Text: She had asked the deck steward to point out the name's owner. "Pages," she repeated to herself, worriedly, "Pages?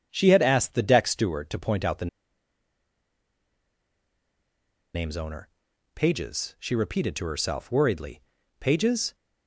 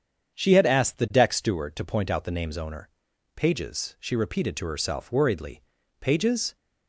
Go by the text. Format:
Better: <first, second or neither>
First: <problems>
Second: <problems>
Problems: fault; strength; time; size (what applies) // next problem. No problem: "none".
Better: second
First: starts louder than the rest; strong; until 1.1 s; 7.5 dB // pauses between "the" and "name's"; strong; at 2.0 s; 2.8 s long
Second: starts louder than the rest; strong; until 1.4 s; 7.5 dB